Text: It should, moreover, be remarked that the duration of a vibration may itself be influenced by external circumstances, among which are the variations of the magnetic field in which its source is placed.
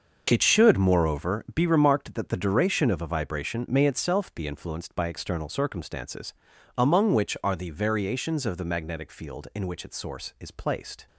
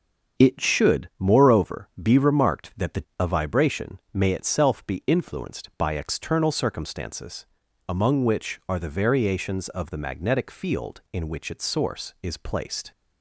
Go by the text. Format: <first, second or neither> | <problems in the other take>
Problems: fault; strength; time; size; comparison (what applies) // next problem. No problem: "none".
first | starts louder than the rest; until 1.4 s; 6.5 dB; noticeable in the first // skips "duration of"; at 3.1 s // pauses between "vibration" and "may"; slight; at 3.9 s; 0.16 s long